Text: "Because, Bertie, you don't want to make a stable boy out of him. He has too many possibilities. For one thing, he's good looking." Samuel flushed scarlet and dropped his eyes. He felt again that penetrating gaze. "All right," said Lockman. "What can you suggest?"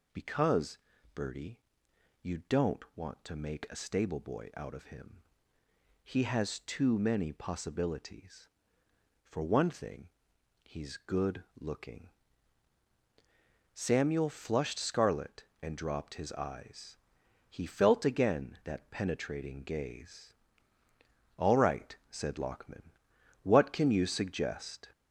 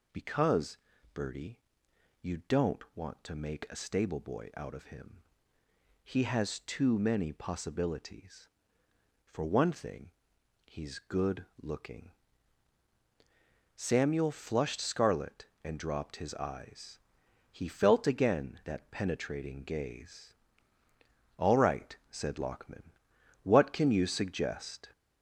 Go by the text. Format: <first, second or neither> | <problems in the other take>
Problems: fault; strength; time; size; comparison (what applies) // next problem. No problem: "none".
neither | pauses between "good" and "looking"; slight; the same in both